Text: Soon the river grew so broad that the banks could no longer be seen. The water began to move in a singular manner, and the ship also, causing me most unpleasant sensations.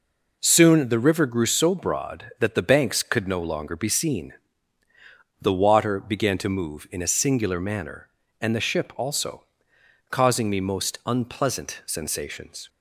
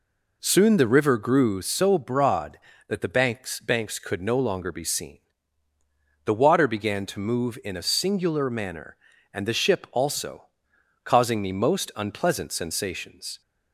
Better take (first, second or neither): first